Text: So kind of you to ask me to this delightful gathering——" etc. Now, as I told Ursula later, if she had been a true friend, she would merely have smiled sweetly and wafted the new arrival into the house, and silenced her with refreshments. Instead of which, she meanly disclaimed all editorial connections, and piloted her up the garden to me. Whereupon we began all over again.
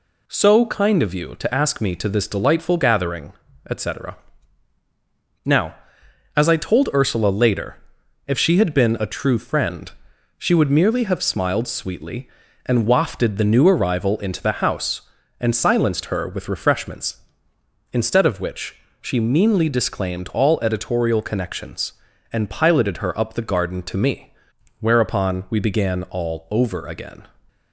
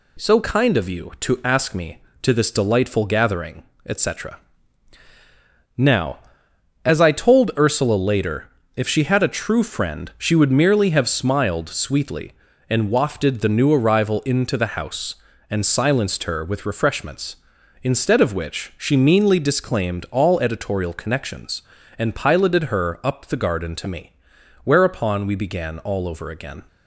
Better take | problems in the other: first | skips "been"; at 9.2 s

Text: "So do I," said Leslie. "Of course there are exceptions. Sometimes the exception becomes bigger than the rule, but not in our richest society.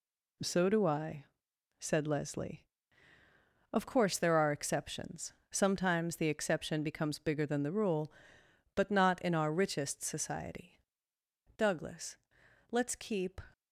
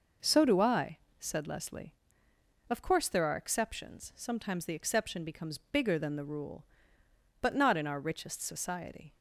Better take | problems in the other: second | goes on to say "Douglas let's keep"; strong; from 11.5 s on; 1.8 s long

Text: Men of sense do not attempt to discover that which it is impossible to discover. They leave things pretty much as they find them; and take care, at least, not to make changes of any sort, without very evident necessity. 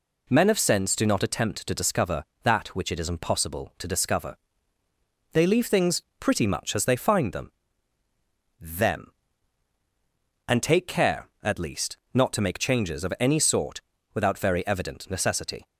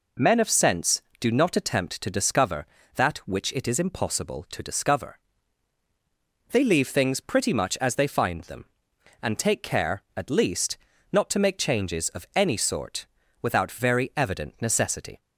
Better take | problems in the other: second | pauses between "things" and "pretty"; slight; at 6.0 s; 0.18 s long // says "them" twice; at 8.6 s

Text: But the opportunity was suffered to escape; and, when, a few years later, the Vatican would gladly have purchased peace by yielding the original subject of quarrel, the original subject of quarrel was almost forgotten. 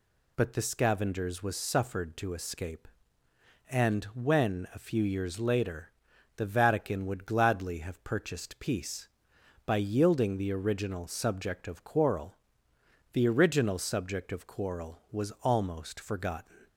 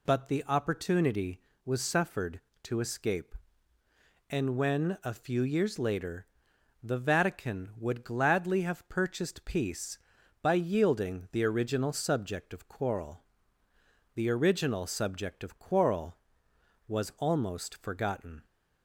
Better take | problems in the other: second | says "scavengers" for "opportunity"; at 0.6 s

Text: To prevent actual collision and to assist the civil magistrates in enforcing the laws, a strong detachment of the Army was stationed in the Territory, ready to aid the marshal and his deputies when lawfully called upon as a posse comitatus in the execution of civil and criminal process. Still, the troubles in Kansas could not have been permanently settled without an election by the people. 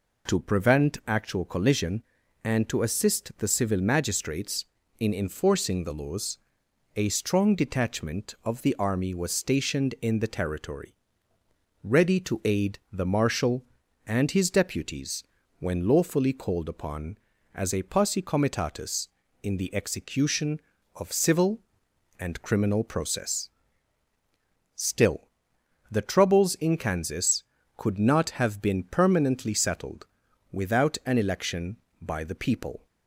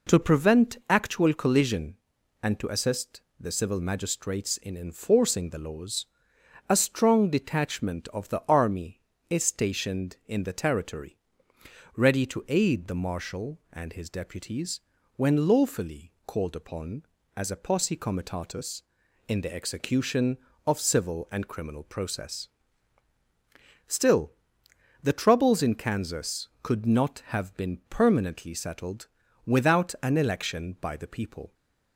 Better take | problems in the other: first | pauses between "assist" and "the"; slight; at 3.1 s; 0.18 s long // says "is" for "was"; at 9.2 s // pauses between "deputies" and "when"; at 14.7 s; 0.38 s long; also in the first // pauses between "settled" and "without"; at 29.0 s; 0.38 s long; noticeable in the first

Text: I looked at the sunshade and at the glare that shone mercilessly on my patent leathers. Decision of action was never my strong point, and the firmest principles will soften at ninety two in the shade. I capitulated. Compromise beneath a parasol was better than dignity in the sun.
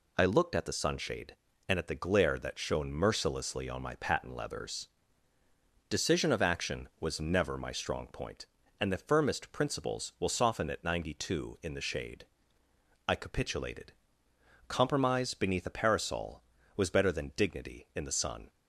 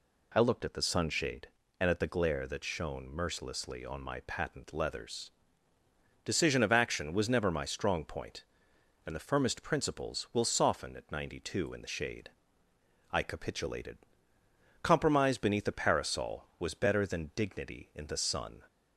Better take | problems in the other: neither | none

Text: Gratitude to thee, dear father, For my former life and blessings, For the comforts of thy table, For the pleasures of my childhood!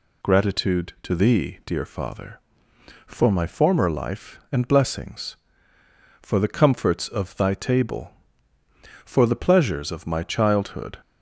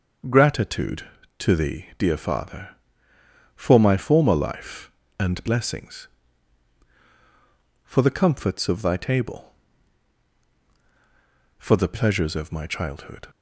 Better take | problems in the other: neither | none

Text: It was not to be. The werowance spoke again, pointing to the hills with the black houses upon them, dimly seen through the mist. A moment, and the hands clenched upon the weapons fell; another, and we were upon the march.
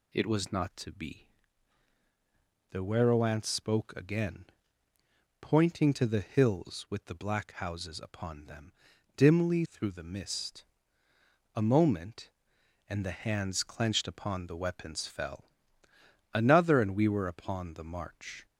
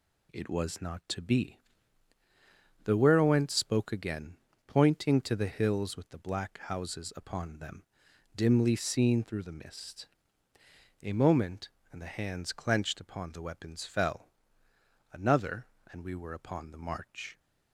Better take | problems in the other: second | skips "seen"; at 9.6 s

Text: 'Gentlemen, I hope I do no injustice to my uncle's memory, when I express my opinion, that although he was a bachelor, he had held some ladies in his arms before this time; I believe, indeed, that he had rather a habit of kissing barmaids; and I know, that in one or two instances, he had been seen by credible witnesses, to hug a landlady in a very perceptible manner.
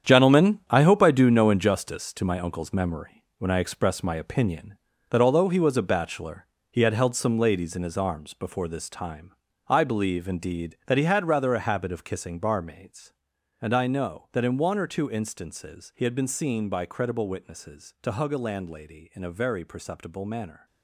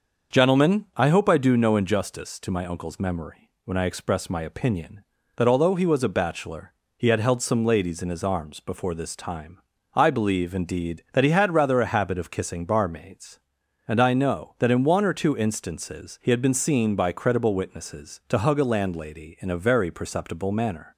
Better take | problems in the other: second | gets quieter; strong; throughout; 10.5 dB // starts louder than the rest; strong; until 1.1 s; 8.5 dB; also in the second

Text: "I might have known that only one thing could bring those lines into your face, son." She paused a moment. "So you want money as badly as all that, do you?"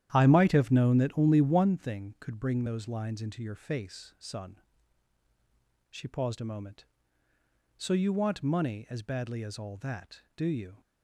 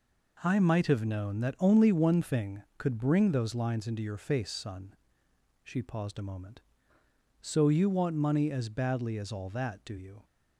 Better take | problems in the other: second | starts louder than the rest; strong; until 1.7 s; 11 dB

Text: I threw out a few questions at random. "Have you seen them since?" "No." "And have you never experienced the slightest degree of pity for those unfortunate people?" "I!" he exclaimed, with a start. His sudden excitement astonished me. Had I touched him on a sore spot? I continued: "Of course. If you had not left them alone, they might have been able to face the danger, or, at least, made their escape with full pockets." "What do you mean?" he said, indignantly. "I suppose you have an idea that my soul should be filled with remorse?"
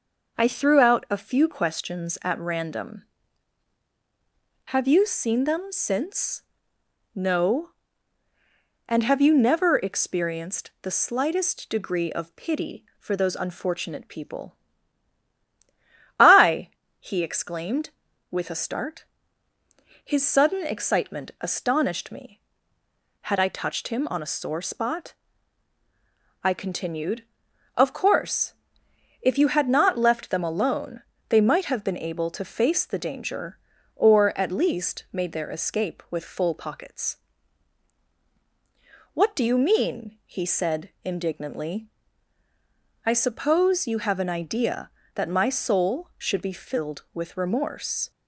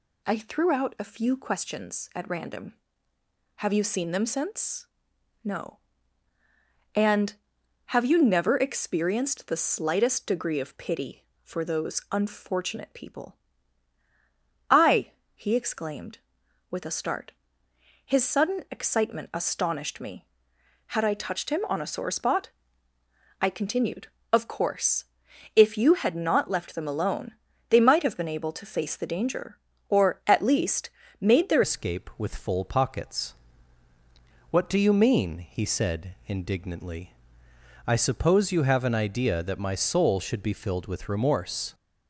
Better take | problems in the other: first | changes voice at "escape"; from 31.6 s on; 10.1 s long

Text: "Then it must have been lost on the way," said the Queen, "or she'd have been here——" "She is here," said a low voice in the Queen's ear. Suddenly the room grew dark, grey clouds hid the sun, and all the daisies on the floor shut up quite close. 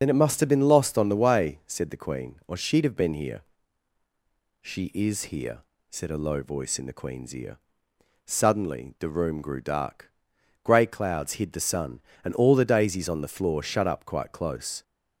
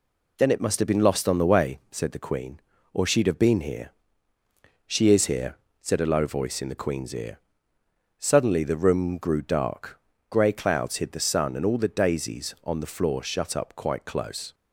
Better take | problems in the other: second | loses the start of "Then"; at 0.0 s; 50 ms // starts louder than the rest; until 1.0 s; 6.5 dB

